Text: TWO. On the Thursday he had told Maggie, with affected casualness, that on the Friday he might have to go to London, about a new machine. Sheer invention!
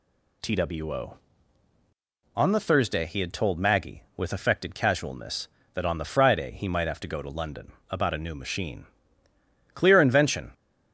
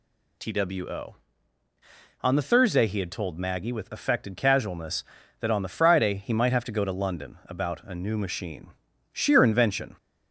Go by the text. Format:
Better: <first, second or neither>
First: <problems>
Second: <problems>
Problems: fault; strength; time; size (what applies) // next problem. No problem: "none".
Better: second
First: says "Clear" for "Sheer"; at 9.7 s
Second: none